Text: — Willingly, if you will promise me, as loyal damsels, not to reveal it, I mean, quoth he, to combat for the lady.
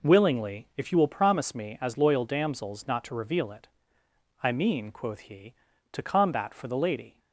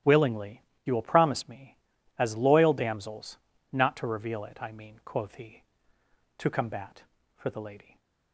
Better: first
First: none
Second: starts louder than the rest; strong; until 1.2 s; 12 dB // skips "if"; at 0.7 s

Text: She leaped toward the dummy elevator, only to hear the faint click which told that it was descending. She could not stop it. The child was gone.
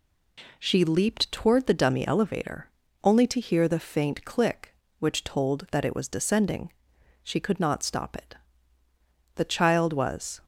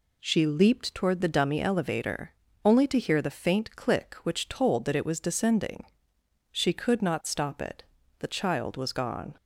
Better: second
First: stops before "gone"; at 10.4 s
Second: none

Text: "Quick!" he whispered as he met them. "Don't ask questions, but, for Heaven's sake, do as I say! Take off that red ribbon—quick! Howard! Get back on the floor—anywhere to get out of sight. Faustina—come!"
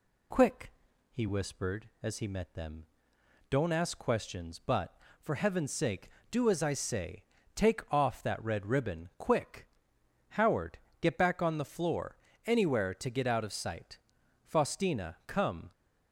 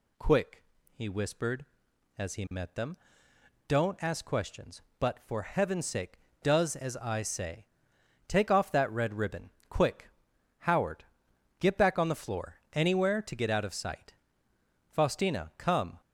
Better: first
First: none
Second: says "does" for "do"; at 6.4 s

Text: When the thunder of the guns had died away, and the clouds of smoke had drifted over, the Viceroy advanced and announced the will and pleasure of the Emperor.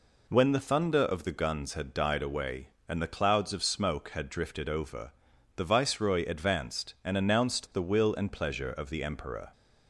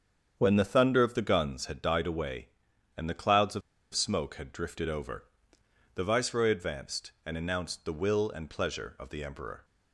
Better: first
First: none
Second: starts louder than the rest; strong; until 1.3 s; 7.5 dB // pauses between "of" and "smoke"; slight; at 3.6 s; 0.33 s long

